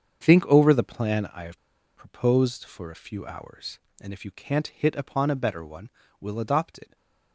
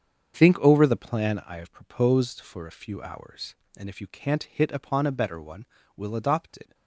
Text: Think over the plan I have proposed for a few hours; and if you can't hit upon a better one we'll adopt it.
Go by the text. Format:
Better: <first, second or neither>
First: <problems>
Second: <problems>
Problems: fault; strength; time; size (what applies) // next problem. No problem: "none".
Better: second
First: starts louder than the rest; strong; until 1.2 s; 7 dB // pauses between "have" and "proposed"; at 1.5 s; 0.37 s long // pauses between "one" and "we'll"; slight; at 5.8 s; 0.30 s long // stays silent after the last word; slight; from 6.8 s on; 0.5 s long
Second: starts louder than the rest; strong; until 1.3 s; 7 dB // pauses between "one" and "we'll"; slight; at 5.6 s; 0.30 s long